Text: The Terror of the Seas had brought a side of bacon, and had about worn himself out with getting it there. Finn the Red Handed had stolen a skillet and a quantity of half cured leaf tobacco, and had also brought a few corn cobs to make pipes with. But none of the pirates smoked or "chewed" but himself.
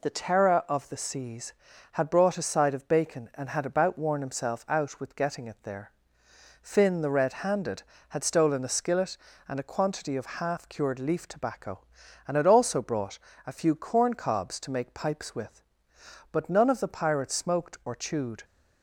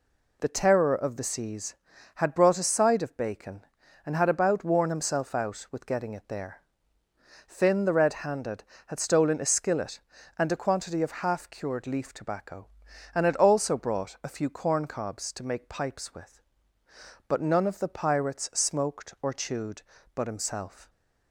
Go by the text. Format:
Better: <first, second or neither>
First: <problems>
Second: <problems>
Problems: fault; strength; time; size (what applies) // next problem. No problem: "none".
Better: second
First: pauses between "brought" and "a"; slight; at 13.1 s; 0.28 s long // stops before "but himself"; at 18.4 s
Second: none